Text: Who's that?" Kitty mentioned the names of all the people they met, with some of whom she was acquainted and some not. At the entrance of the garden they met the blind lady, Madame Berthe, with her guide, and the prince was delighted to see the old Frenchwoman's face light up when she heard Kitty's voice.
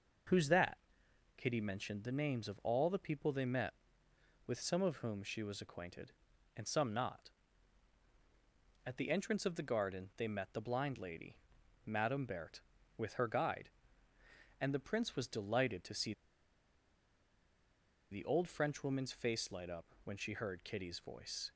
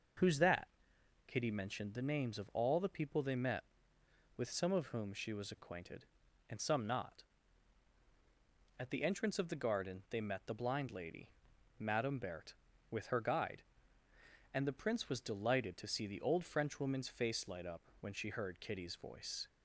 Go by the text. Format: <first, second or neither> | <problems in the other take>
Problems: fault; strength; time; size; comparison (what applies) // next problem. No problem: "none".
second | pauses between "see" and "the"; strong; at 16.1 s; 1.9 s long // pauses between "up" and "when"; slight; at 19.8 s; 0.20 s long; slight in the second